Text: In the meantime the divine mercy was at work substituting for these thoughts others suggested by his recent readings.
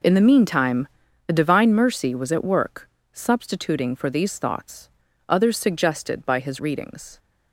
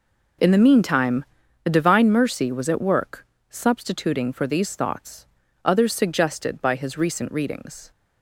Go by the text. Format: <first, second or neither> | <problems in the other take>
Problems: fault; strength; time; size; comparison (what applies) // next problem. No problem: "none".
second | pauses between "meantime" and "the"; at 0.8 s; 0.40 s long; also in the second // pauses between "work" and "substituting"; slight; at 2.8 s; 0.24 s long; slight in the second // pauses between "thoughts" and "others"; at 4.8 s; 0.40 s long; also in the second // skips "recent"; at 6.6 s